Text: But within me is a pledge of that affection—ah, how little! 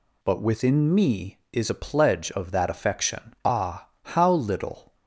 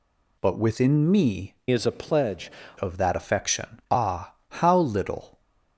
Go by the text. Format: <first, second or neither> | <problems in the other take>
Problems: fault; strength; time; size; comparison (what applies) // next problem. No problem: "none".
first | changes voice from "is" to "pledge"; from 1.7 to 2.5 s; 0.8 s long